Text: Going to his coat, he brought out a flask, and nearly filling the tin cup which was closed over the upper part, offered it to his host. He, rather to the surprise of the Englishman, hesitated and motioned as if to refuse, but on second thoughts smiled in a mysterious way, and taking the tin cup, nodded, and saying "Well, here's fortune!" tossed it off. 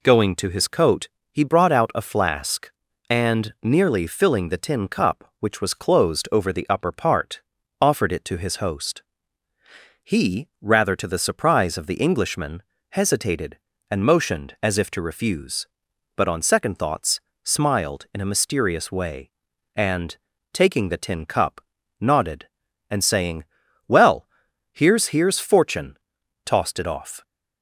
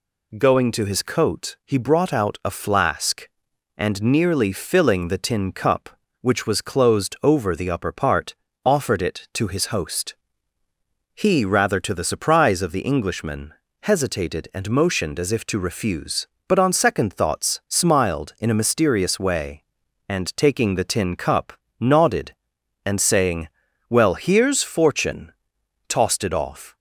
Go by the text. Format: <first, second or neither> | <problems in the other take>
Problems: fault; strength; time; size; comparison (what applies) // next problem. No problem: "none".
second | pauses between "thoughts" and "smiled"; slight; at 17.1 s; 0.24 s long // pauses between "and" and "taking"; slight; at 20.1 s; 0.36 s long // pauses between "saying" and "Well"; at 23.4 s; 0.44 s long; also in the second // says "here's" twice; at 25.0 s